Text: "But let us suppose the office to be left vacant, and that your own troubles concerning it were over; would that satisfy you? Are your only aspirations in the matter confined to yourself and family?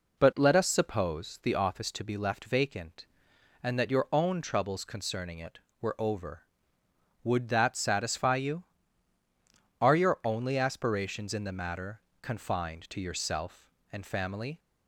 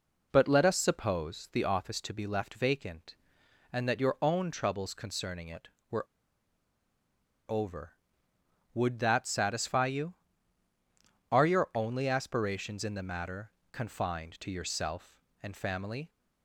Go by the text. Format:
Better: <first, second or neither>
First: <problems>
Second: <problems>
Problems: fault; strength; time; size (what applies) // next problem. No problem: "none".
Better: first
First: pauses between "matter" and "confined"; slight; at 12.0 s; 0.18 s long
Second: pauses between "were" and "over"; strong; at 6.0 s; 1.4 s long // pauses between "matter" and "confined"; slight; at 13.5 s; 0.18 s long